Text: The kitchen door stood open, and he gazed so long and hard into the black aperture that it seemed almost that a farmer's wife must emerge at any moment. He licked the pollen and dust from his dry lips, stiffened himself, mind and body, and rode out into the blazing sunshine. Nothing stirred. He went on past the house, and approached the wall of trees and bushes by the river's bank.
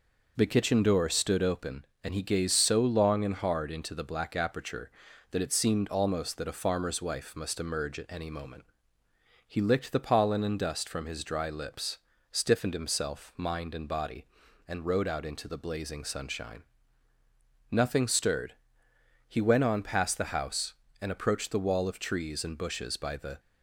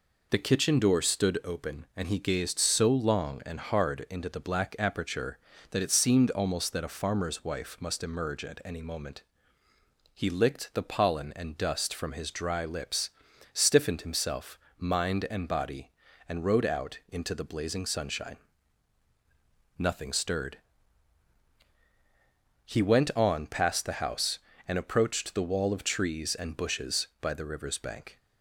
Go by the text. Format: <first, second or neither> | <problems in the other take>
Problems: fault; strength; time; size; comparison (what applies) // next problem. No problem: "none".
second | stops before "river's bank"; at 23.3 s